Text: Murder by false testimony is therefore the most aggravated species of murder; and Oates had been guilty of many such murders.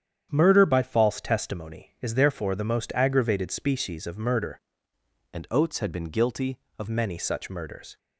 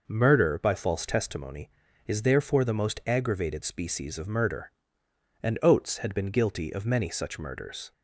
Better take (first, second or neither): second